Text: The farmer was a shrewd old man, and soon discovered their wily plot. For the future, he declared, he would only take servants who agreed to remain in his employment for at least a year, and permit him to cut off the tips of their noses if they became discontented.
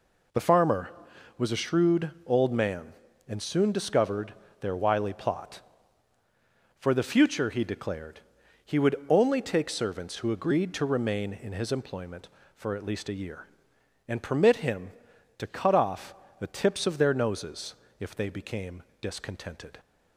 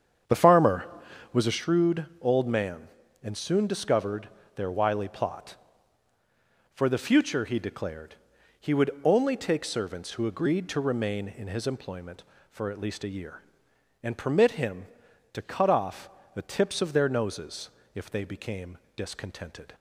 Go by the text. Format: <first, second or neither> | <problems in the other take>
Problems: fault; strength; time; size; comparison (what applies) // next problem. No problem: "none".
first | starts louder than the rest; strong; until 1.6 s; 8 dB // pauses between "discovered" and "their"; slight; at 4.2 s; 0.26 s long; slight in the first // pauses between "off" and "the"; slight; at 16.0 s; 0.24 s long; slight in the first // pauses between "noses" and "if"; slight; at 17.6 s; 0.24 s long; slight in the first // pauses between "became" and "discontented"; slight; at 18.7 s; 0.18 s long; slight in the first